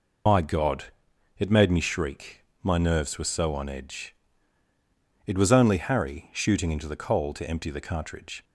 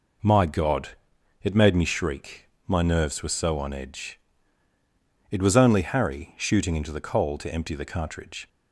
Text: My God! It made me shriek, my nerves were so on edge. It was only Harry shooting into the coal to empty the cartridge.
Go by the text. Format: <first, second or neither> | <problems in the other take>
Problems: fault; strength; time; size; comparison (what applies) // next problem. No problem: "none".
second | loses the start of "My"; at 0.2 s; 80 ms